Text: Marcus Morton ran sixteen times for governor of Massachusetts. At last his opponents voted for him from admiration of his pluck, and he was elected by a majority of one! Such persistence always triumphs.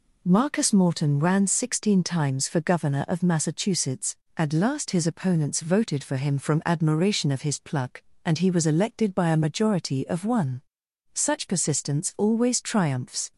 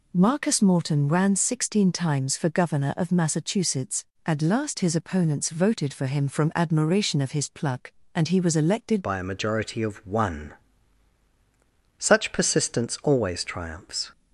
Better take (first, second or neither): first